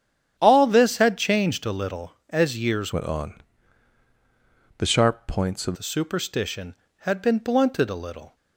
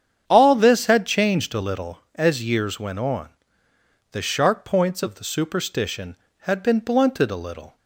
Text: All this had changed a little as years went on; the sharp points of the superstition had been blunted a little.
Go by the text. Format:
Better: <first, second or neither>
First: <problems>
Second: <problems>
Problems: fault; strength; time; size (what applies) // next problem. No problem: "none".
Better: second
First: starts louder than the rest; strong; until 1.3 s; 9 dB // changes voice from "went" to "of"; from 2.9 to 5.7 s; 2.8 s long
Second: starts louder than the rest; strong; until 1.2 s; 8 dB